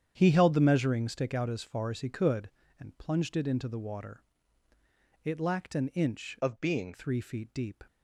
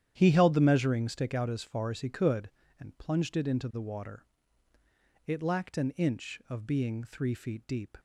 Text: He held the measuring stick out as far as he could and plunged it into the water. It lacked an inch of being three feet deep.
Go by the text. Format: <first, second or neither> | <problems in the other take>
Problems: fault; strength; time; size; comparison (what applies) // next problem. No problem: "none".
second | starts louder than the rest; strong; until 1.1 s; 9 dB; strong in the second // changes voice from "of" to "being"; from 6.4 to 6.9 s; 0.5 s long